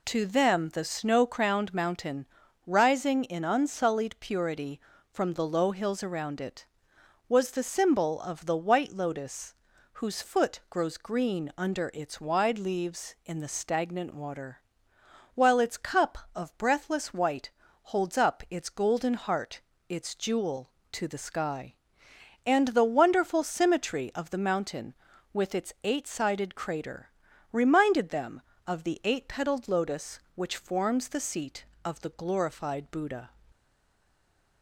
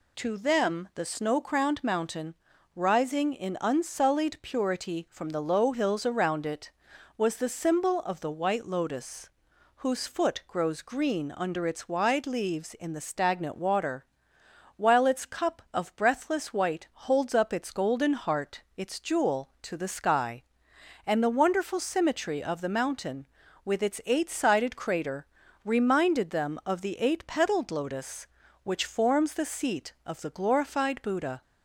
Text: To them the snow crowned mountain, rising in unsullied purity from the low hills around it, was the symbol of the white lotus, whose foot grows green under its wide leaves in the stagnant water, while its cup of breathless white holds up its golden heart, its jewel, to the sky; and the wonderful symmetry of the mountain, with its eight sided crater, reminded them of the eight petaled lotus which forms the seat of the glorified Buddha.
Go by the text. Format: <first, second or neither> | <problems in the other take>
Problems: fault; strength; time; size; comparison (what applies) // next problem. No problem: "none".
second | pauses between "white" and "holds"; slight; at 17.4 s; 0.34 s long // stays silent after the last word; from 33.5 s on; 1.1 s long